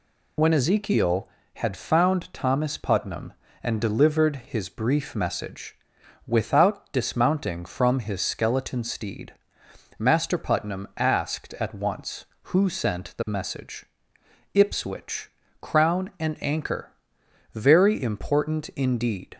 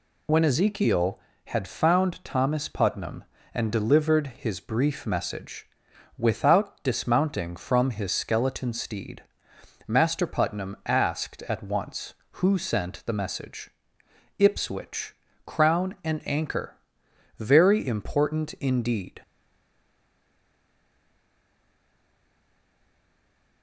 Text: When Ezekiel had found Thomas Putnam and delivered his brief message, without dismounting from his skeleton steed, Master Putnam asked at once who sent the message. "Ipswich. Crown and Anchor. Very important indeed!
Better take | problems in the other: first | stays silent after the last word; strong; from 19.2 s on; 4.4 s long

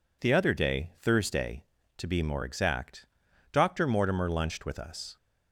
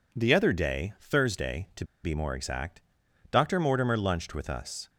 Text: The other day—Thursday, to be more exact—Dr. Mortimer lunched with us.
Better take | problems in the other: first | pauses between "to" and "be"; slight; at 1.8 s; 0.18 s long

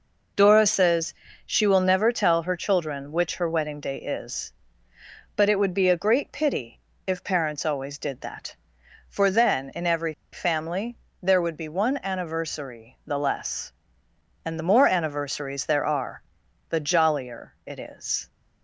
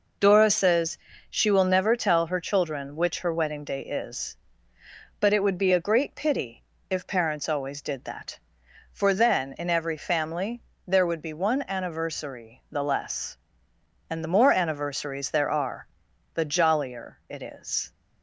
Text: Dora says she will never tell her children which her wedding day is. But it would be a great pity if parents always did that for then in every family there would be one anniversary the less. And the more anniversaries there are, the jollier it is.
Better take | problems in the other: second | pauses between "says" and "she"; slight; at 1.1 s; 0.32 s long; slight in the second // pauses between "pity" and "if"; slight; at 6.7 s; 0.26 s long; slight in the second // pauses between "every" and "family"; slight; at 10.1 s; 0.18 s long // pauses between "family" and "there"; slight; at 10.9 s; 0.24 s long; slight in the second

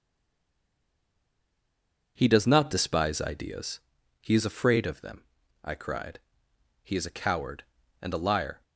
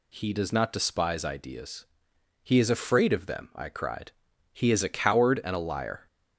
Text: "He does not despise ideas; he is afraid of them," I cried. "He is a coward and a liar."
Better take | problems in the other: second | stays silent before the first word; until 2.1 s; 2.1 s long

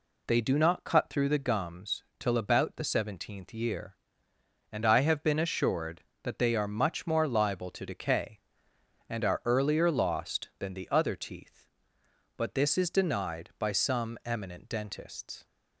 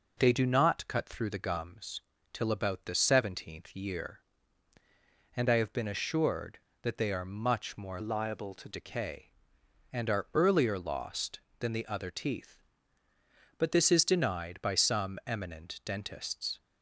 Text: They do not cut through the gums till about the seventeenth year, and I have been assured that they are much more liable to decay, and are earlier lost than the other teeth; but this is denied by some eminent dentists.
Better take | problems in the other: first | pauses between "gums" and "till"; slight; at 2.0 s; 0.32 s long; slight in the first // changes voice from "liable" to "to"; from 7.9 to 8.6 s; 0.7 s long

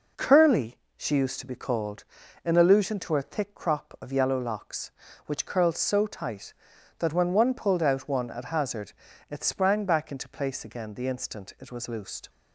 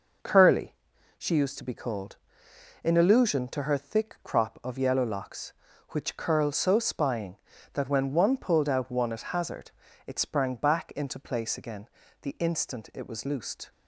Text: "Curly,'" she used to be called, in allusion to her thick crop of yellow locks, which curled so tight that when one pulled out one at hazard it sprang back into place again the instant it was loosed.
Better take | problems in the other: first | says "spying" for "tight"; at 6.7 s // pauses between "hazard" and "it"; slight; at 9.7 s; 0.36 s long; slight in the first // pauses between "again" and "the"; slight; at 11.8 s; 0.32 s long

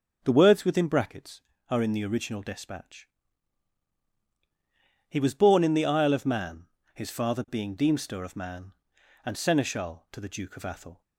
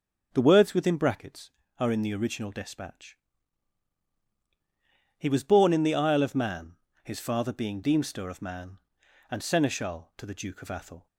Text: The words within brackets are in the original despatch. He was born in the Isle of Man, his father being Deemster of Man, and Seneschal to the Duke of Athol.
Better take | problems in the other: neither | starts louder than the rest; the same in both

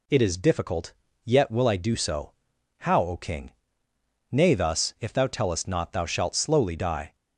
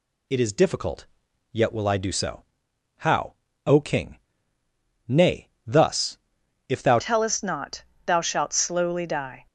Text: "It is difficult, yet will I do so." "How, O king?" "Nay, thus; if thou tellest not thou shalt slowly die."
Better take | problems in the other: first | changes voice at "tellest"; from 6.9 s on; 2.5 s long // pauses between "not" and "thou"; slight; at 7.8 s; 0.22 s long

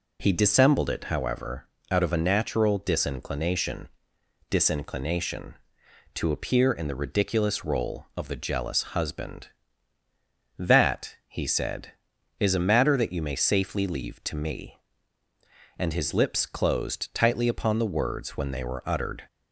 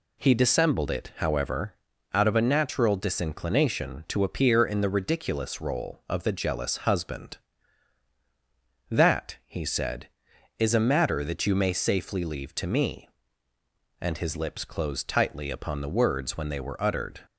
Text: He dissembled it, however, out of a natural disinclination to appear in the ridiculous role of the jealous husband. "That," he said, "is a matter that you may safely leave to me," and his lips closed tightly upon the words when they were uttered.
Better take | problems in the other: second | says "disinclination" twice; at 4.5 s

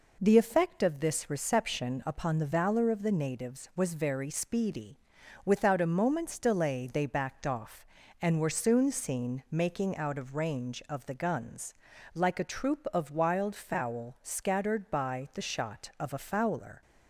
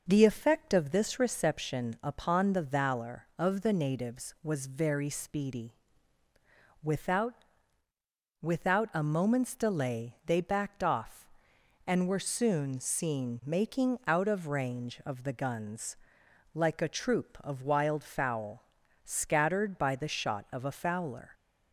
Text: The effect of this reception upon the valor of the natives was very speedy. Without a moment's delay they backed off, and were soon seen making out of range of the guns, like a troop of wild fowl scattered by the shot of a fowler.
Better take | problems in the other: first | says "Without" twice; at 8.4 s // pauses between "fowl" and "scattered"; at 18.6 s; 0.40 s long

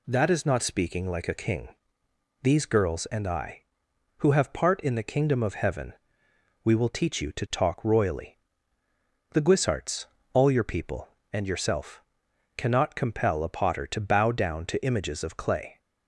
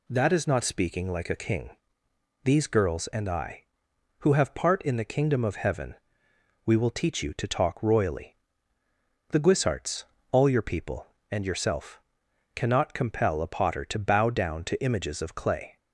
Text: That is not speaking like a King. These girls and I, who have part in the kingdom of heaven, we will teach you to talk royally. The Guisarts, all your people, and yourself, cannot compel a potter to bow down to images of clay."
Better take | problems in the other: neither | none

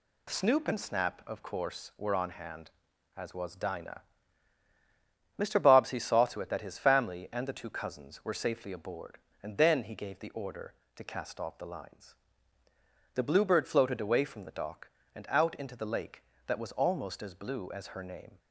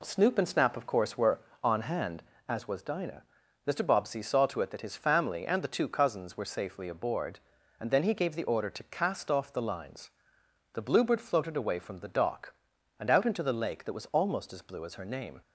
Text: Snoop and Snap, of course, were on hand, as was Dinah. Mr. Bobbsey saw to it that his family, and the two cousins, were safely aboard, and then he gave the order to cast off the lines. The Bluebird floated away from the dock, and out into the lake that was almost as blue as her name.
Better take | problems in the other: neither | none

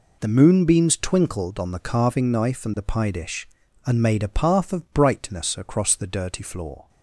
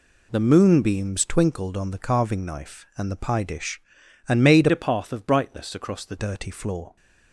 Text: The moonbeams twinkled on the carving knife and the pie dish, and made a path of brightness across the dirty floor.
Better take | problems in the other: first | changes voice from "a" to "the"; from 4.7 to 6.1 s; 1.4 s long

